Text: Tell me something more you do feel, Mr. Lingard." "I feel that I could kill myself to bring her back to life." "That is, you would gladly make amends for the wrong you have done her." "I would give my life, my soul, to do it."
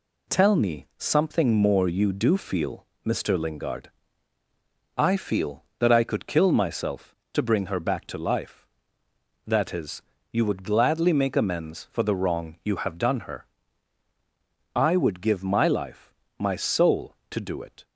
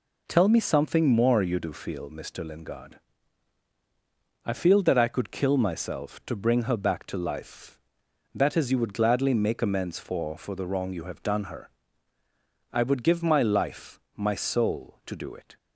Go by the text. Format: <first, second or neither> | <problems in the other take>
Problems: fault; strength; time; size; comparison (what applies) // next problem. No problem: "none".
first | says "for" twice; at 10.3 s